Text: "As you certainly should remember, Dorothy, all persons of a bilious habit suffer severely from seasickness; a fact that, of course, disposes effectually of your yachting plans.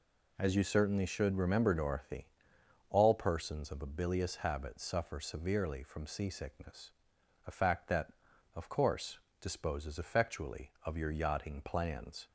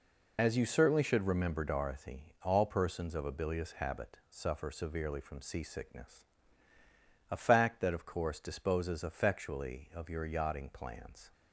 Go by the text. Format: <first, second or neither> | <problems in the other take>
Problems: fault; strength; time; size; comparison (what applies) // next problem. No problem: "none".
first | loses the start of "As"; at 0.3 s; 80 ms